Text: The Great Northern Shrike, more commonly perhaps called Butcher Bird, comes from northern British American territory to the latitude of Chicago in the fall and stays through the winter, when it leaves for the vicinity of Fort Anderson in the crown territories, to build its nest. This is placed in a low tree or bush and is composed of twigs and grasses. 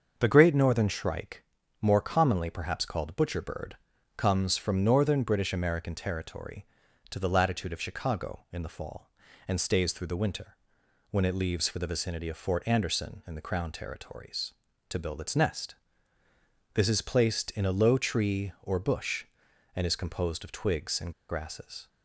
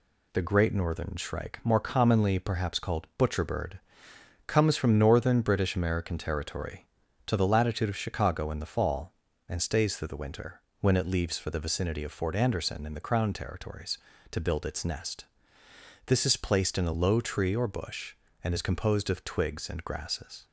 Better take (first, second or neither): second